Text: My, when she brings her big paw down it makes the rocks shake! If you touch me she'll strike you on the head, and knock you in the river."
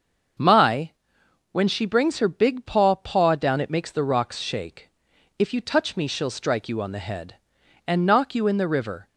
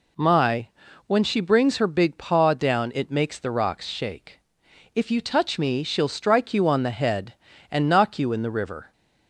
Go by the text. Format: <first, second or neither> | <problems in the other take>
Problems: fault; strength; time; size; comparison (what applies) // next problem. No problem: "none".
second | starts louder than the rest; until 1.9 s; 6.5 dB // says "paw" twice; at 2.9 s